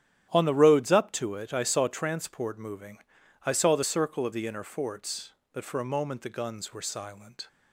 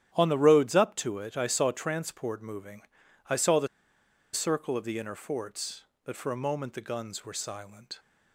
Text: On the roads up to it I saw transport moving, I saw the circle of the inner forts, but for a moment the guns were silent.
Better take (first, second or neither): first